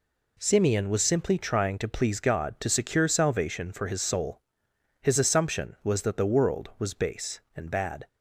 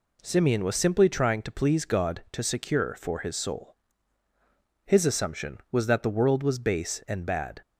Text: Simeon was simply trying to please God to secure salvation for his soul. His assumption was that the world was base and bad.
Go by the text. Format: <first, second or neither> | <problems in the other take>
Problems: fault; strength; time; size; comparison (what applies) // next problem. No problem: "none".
first | skips "salvation"; at 2.9 s